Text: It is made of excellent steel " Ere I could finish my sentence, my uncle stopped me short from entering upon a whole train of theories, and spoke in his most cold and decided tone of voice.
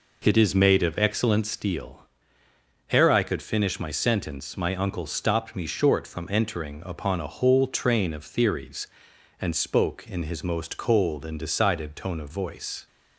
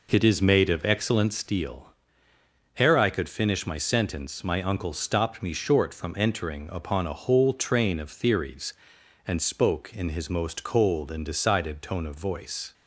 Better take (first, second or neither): neither